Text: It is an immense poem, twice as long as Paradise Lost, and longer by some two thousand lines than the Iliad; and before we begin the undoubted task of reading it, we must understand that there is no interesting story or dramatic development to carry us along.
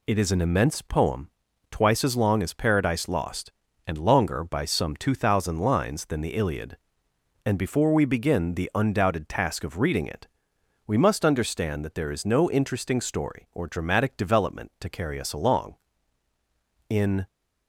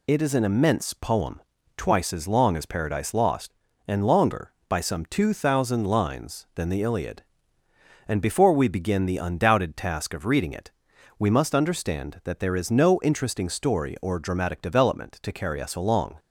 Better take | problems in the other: second | goes on to say "In"; slight; from 16.8 s on; 0.38 s long

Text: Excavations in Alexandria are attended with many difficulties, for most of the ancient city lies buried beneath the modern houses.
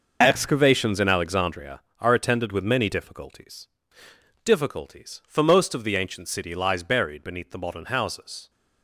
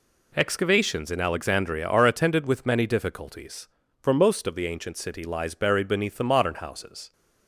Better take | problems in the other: second | says "difficulties" twice; at 4.4 s

